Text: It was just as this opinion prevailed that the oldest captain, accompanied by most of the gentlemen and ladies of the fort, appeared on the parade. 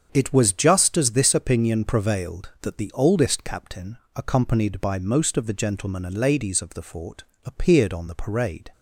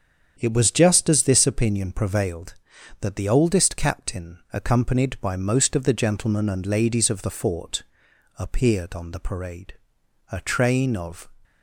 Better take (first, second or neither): first